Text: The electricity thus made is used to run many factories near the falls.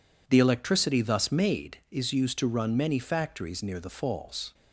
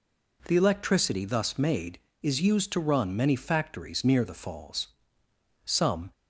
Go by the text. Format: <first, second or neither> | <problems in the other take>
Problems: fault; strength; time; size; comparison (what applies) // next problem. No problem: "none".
first | goes on to say "Some"; slight; from 5.6 s on; 0.46 s long